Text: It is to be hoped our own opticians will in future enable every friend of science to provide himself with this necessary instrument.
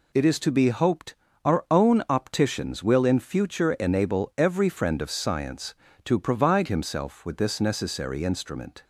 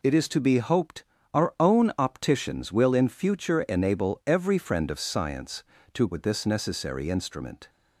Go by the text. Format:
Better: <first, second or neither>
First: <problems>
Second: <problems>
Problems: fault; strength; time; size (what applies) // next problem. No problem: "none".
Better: first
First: pauses between "hoped" and "our"; slight; at 1.1 s; 0.30 s long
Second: pauses between "hoped" and "our"; slight; at 1.0 s; 0.30 s long // skips "provide himself"; at 6.0 s